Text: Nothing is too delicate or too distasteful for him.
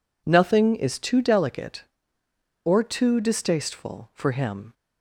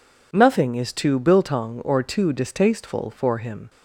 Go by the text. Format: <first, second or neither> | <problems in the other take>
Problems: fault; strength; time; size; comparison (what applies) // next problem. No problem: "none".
first | says "biltong" for "delicate"; at 1.1 s